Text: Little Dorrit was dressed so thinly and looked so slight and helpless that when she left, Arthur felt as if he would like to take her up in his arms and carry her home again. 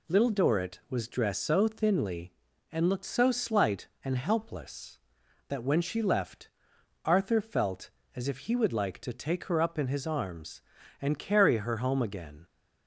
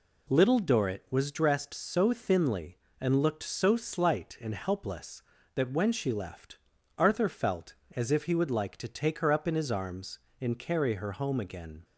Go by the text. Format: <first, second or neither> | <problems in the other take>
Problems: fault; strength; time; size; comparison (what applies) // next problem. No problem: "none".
neither | none